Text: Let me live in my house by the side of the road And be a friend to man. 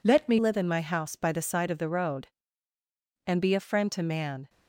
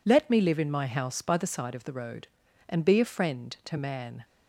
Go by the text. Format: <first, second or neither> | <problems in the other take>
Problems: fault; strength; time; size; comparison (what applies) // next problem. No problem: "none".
second | changes voice at "live"; from 0.3 s on; 4.1 s long